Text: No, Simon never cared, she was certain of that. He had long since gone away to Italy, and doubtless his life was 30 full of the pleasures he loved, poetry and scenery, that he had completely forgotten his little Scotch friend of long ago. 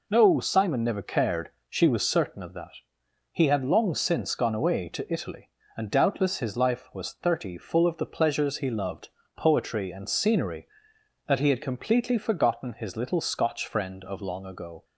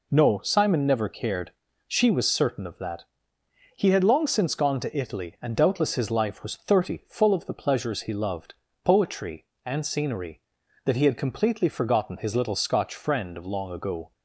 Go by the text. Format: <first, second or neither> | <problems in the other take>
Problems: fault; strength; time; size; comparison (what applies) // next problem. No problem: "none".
first | skips "away"; at 4.7 s